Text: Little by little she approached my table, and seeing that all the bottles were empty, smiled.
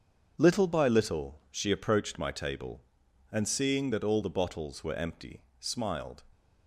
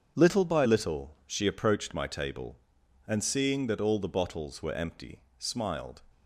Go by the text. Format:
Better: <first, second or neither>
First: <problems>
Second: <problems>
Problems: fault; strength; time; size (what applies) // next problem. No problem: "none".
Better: neither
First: starts louder than the rest; until 1.4 s; 7 dB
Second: starts louder than the rest; until 1.2 s; 7 dB